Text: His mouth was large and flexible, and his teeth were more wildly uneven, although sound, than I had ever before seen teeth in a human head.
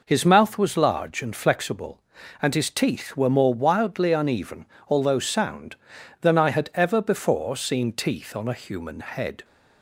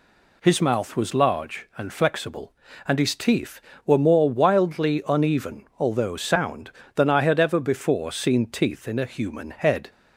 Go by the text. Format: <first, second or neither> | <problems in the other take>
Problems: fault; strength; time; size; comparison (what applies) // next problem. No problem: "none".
second | says "on" for "in"; at 8.3 s